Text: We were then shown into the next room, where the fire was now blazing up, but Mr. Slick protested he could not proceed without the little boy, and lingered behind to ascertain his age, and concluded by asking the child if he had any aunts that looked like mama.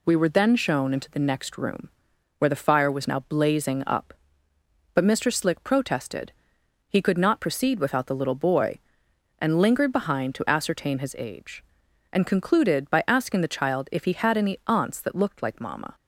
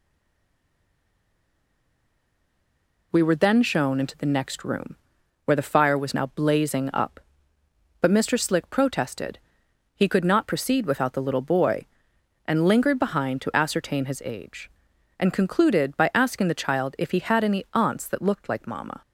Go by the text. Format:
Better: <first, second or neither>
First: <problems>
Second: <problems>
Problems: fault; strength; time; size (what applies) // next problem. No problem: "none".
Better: first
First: pauses between "protested" and "he"; noticeable; at 6.3 s; 0.56 s long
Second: stays silent before the first word; strong; until 3.1 s; 3.1 s long // pauses between "protested" and "he"; noticeable; at 9.3 s; 0.56 s long